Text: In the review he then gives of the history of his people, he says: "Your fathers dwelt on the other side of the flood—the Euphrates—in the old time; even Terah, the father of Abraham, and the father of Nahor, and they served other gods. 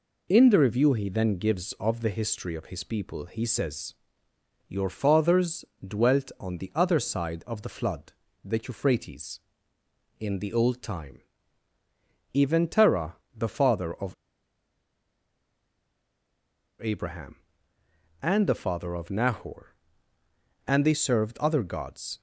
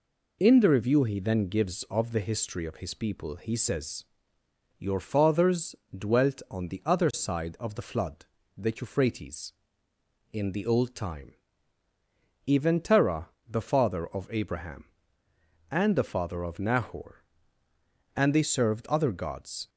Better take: second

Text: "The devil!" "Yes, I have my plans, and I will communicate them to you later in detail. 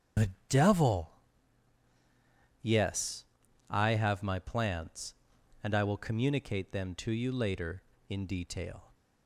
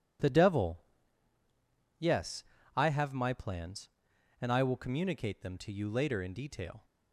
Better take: second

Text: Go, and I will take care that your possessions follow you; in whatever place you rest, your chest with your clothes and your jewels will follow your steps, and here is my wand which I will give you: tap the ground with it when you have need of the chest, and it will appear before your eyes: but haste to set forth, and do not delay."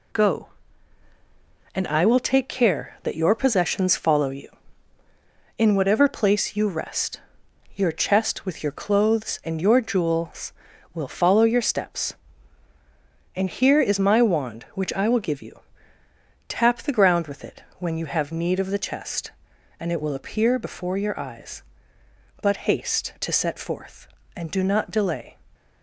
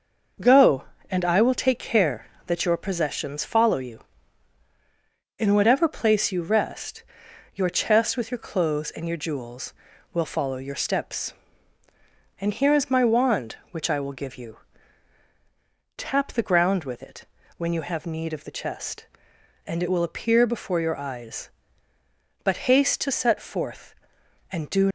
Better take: first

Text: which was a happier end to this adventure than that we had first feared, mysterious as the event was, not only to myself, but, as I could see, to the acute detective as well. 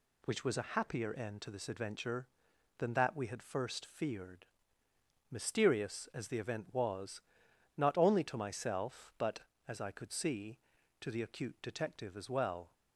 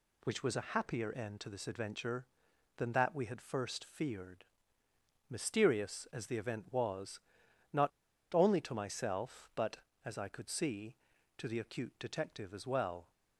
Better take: first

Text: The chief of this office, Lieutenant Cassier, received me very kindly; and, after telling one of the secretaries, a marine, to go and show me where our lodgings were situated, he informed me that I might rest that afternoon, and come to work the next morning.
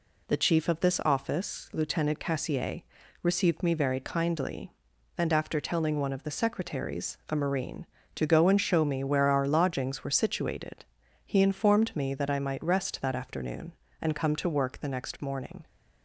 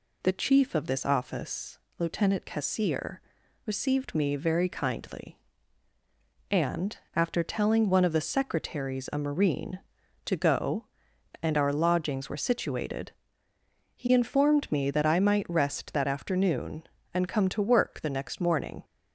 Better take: first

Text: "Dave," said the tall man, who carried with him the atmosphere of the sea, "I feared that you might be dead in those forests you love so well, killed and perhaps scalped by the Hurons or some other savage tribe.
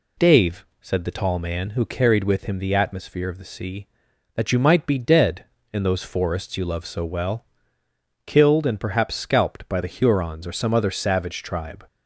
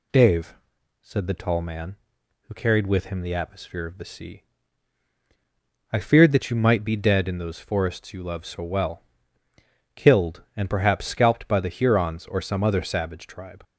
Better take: second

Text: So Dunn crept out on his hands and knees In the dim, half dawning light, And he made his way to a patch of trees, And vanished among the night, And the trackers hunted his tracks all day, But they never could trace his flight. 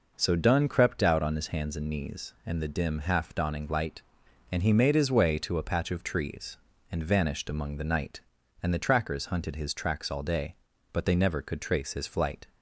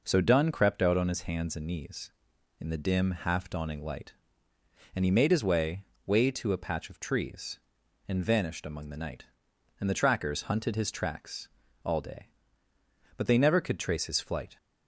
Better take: first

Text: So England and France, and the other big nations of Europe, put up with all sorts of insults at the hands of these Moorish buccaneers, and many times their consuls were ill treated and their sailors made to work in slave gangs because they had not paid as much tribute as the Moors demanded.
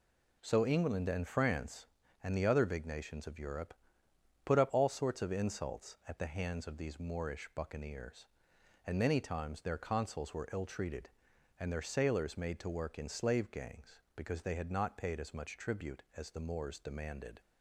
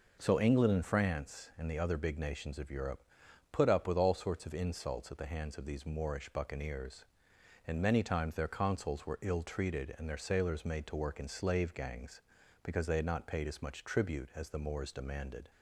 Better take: second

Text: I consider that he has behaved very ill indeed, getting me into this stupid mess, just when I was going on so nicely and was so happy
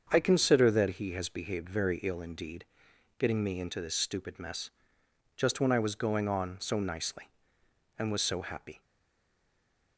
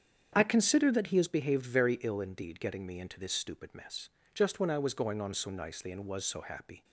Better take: second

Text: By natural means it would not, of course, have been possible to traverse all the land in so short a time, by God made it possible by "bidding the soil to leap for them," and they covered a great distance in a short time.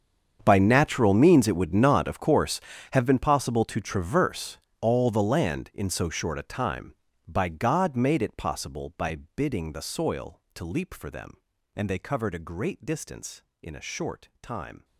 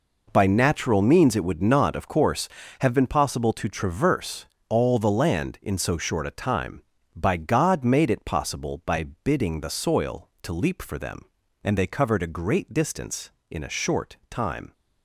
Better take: second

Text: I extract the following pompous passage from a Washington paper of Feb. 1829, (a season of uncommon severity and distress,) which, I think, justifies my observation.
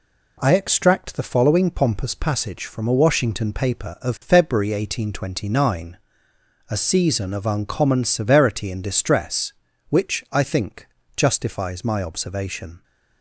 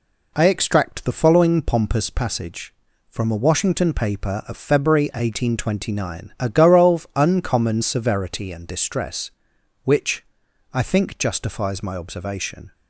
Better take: first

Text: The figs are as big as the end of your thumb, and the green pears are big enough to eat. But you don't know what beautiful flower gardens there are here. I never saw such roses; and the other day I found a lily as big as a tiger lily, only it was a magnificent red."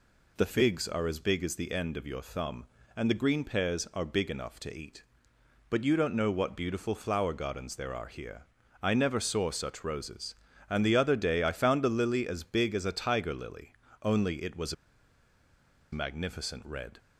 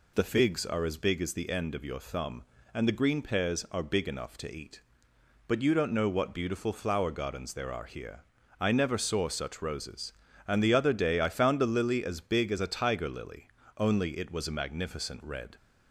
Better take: second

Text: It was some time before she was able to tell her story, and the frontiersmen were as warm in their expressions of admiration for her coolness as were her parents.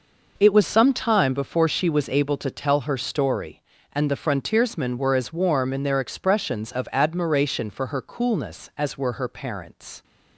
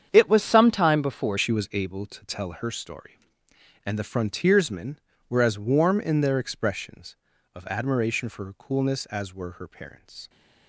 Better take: first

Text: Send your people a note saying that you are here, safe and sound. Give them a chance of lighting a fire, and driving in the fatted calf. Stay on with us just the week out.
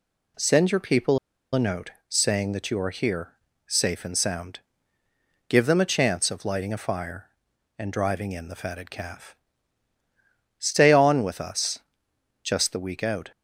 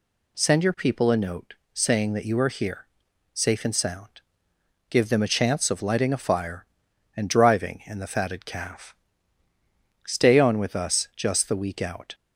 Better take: second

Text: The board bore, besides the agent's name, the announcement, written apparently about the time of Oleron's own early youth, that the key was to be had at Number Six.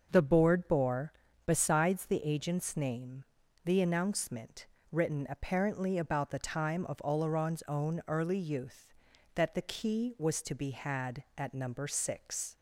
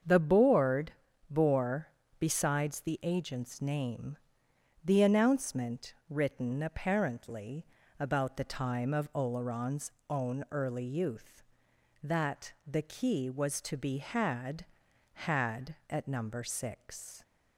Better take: first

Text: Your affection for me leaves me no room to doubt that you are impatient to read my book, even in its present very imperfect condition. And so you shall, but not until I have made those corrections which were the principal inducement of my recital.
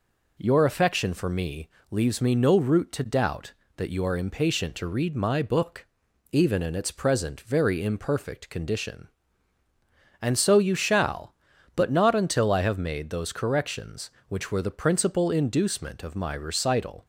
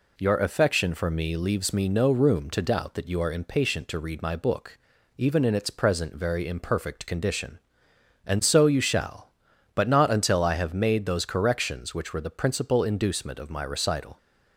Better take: second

